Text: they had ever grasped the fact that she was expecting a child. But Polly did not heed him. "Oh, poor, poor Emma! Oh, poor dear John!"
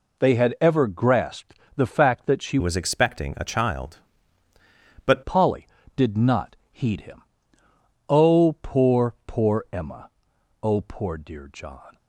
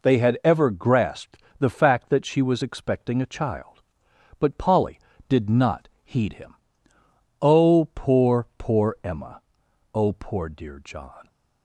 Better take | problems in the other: second | pauses between "grasped" and "the"; slight; at 1.5 s; 0.18 s long; slight in the second // changes voice from "was" to "But"; from 2.5 to 5.2 s; 2.7 s long // pauses between "not" and "heed"; slight; at 6.5 s; 0.16 s long; slight in the second

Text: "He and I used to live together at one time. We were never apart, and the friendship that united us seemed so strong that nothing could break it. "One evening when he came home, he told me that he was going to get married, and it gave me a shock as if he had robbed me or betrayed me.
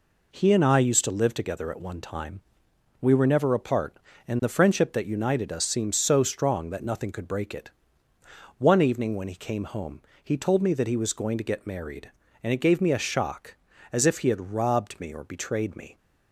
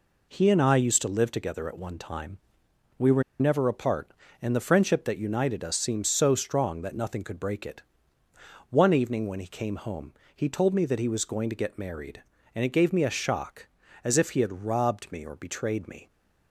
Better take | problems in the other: first | pauses between "were" and "never"; slight; at 3.2 s; 0.18 s long

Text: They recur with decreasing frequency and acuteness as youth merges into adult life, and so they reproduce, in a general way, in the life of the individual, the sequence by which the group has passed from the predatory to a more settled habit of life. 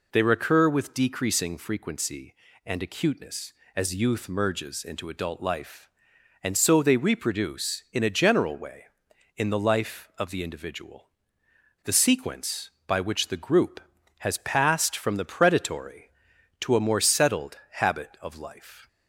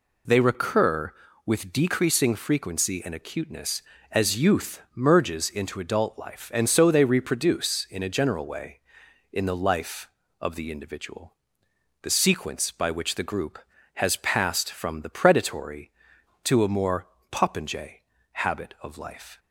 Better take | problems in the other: first | says "popinjay" for "settled"; at 17.3 s

